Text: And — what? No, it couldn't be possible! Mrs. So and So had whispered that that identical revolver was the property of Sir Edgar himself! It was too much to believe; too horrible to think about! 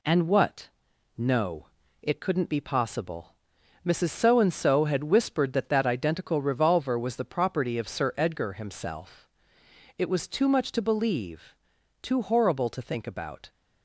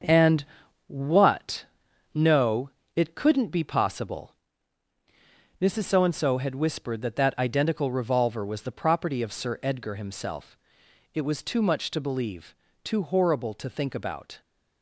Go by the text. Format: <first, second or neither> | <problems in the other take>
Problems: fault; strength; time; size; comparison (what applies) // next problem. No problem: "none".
first | gets quieter; throughout; 7 dB